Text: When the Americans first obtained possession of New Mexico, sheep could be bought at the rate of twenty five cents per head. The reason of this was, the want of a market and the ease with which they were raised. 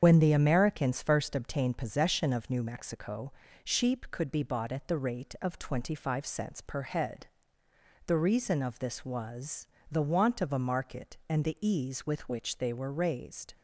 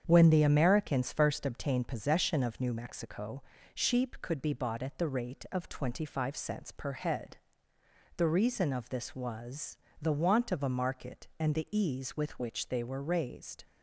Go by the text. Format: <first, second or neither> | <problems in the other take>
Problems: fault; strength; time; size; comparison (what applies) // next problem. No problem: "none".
second | loses the start of "When"; at 0.0 s; 85 ms // starts louder than the rest; strong; until 1.0 s; 7.5 dB; strong in the second